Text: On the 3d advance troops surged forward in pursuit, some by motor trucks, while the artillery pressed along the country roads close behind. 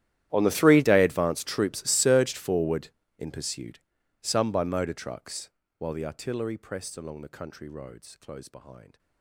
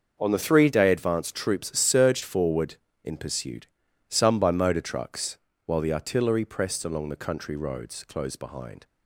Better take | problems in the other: second | gets quieter; strong; throughout; 24.5 dB // starts louder than the rest; strong; until 1.3 s; 12.5 dB; also in the second

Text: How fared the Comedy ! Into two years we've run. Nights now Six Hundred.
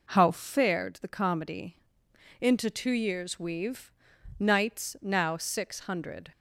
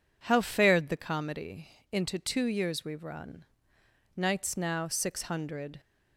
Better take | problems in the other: second | skips "run"; at 4.1 s

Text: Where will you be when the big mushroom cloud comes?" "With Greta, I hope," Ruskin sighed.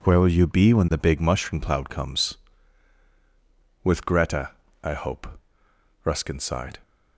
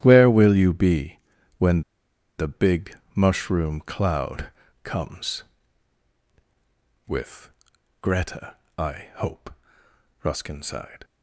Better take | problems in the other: first | starts louder than the rest; strong; until 1.0 s; 12 dB // pauses between "be" and "when"; at 1.1 s; 0.40 s long // pauses between "when" and "the"; noticeable; at 1.8 s; 0.55 s long // pauses between "big" and "mushroom"; slight; at 2.9 s; 0.18 s long // pauses between "cloud" and "comes"; slight; at 4.5 s; 0.34 s long // pauses between "With" and "Greta"; noticeable; at 7.5 s; 0.50 s long

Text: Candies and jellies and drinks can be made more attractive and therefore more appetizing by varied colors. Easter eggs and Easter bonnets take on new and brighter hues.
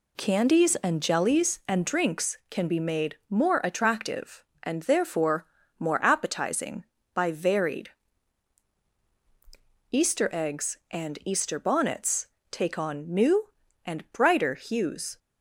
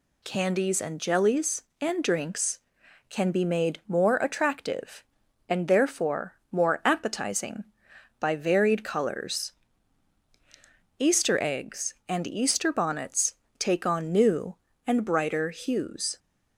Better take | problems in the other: second | pauses between "therefore" and "more"; slight; at 5.4 s; 0.32 s long; slight in the second // skips "colors"; at 8.9 s // pauses between "bonnets" and "take"; slight; at 12.2 s; 0.22 s long; slight in the second

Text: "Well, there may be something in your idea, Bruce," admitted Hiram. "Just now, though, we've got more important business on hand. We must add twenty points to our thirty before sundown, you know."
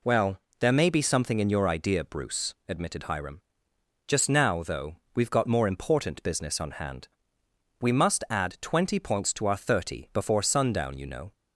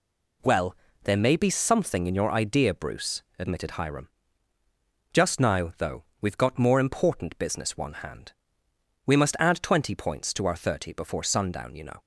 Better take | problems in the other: first | says "one" for "on"; at 7.7 s

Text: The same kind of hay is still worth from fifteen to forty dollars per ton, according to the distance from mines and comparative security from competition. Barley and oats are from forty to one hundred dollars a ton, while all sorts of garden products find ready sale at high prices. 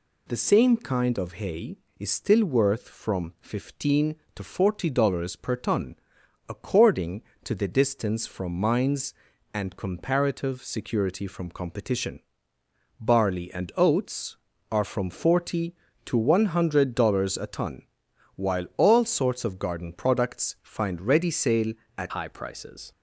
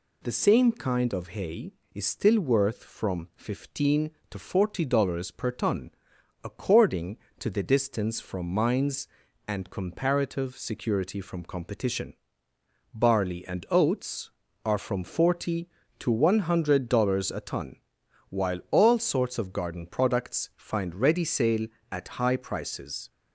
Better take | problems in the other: second | changes voice at "high"; from 22.1 s on; 0.8 s long

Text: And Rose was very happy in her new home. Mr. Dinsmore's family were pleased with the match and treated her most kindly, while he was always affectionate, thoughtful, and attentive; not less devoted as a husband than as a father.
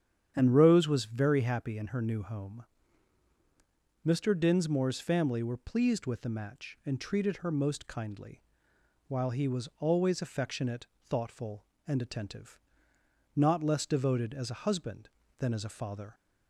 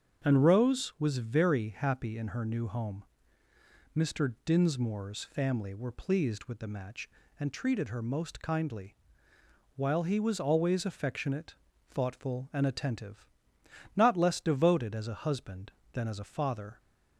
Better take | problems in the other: neither | starts louder than the rest; strong; the same in both

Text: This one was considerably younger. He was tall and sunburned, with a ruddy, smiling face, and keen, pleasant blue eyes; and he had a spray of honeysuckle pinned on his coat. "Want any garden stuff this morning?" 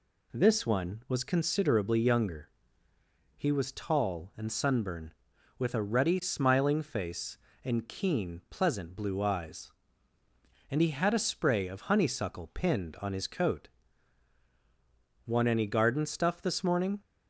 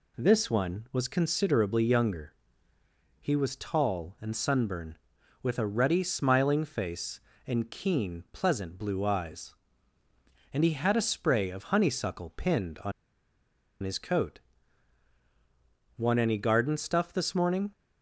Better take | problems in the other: first | pauses between "on" and "his"; noticeable; at 12.9 s; 0.90 s long

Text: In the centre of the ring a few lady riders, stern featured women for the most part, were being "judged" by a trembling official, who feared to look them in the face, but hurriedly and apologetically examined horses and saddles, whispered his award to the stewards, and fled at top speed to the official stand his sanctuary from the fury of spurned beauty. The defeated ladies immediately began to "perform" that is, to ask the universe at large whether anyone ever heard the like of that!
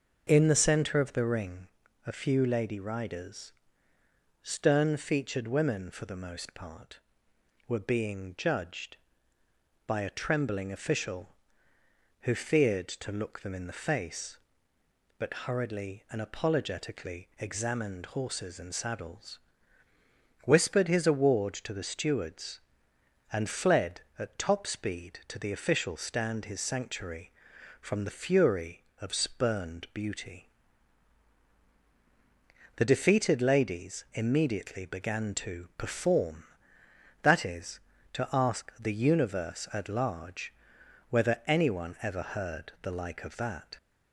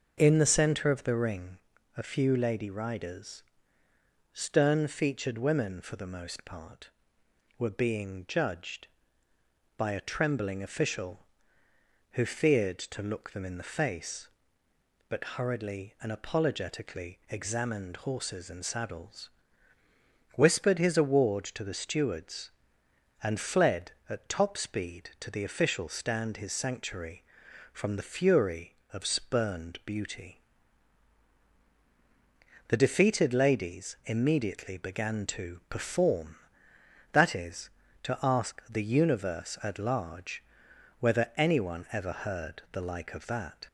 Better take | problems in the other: neither | starts louder than the rest; noticeable; the same in both // pauses between "ring" and "a"; the same in both // pauses between "large" and "whether"; noticeable; the same in both

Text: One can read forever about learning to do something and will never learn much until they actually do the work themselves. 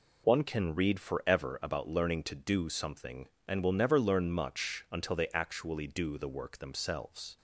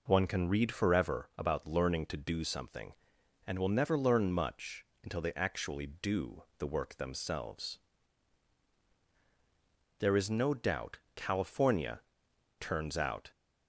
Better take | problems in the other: first | pauses between "much" and "until"; slight; at 4.8 s; 0.18 s long // pauses between "do" and "the"; slight; at 6.4 s; 0.16 s long // goes on to say "There is no doubt California turns out"; strong; from 9.9 s on; 3.3 s long

